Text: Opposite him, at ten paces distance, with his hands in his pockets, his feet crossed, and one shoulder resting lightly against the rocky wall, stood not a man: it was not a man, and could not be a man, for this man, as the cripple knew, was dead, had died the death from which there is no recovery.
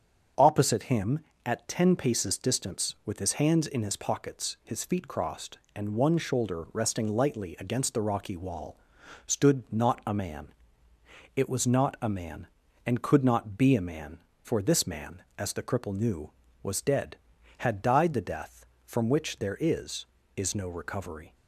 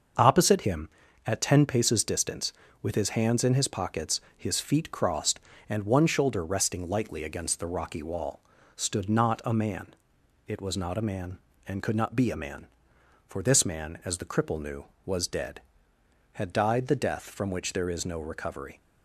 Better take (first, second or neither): second